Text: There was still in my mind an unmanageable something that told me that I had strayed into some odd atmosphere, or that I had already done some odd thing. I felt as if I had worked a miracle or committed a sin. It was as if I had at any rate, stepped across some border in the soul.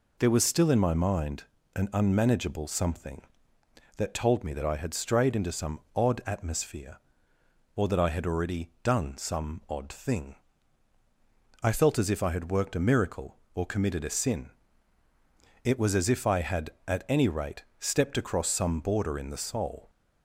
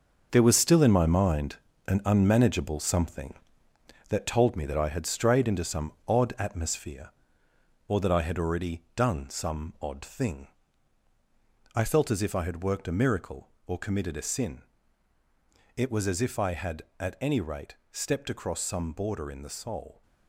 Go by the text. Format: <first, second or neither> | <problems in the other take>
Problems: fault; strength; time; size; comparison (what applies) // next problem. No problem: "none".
first | gets quieter; strong; throughout; 9.5 dB // pauses between "mind" and "an"; slight; at 1.5 s; 0.32 s long; slight in the first // pauses between "some" and "odd"; slight; at 5.9 s; 0.16 s long; slight in the first